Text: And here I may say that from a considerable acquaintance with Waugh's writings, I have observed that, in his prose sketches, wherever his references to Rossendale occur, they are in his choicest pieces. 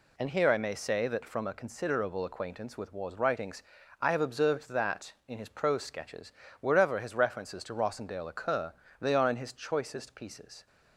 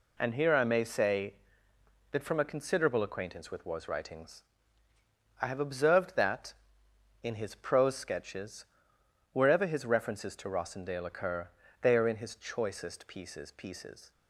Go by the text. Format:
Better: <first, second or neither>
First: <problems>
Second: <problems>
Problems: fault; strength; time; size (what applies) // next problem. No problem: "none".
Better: first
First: none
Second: says "pieces" twice; at 13.5 s